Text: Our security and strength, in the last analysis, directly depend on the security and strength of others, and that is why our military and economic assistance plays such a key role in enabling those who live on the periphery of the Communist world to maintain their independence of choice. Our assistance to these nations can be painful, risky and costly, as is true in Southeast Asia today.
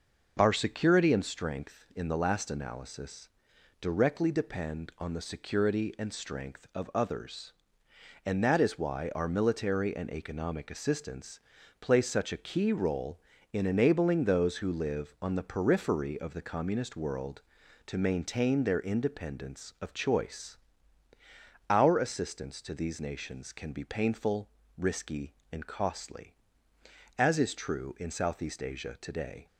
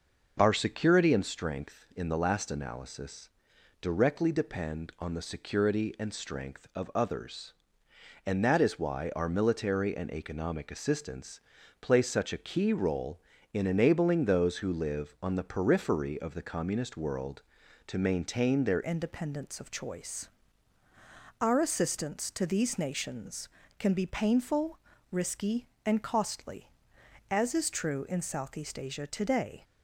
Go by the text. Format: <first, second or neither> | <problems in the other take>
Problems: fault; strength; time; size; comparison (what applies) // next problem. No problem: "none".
first | pauses between "assistance" and "plays"; at 11.4 s; 0.40 s long; also in the first // changes voice at "independence"; from 18.8 s on; 10.8 s long